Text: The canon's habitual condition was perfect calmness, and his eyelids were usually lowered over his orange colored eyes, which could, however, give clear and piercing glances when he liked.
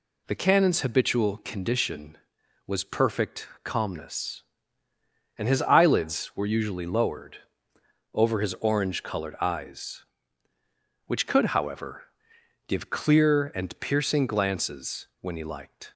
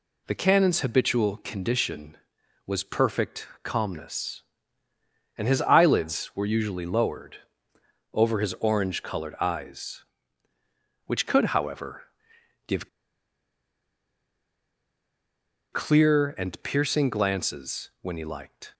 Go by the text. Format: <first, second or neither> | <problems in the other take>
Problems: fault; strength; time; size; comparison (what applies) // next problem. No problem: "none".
first | pauses between "perfect" and "calmness"; slight; at 3.4 s; 0.16 s long; slight in the first // pauses between "lowered" and "over"; noticeable; at 7.3 s; 0.76 s long; noticeable in the first // pauses between "give" and "clear"; strong; at 12.8 s; 2.8 s long